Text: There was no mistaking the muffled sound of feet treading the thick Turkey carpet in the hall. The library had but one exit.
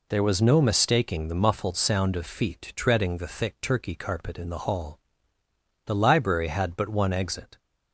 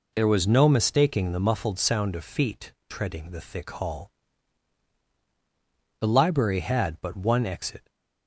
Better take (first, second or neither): first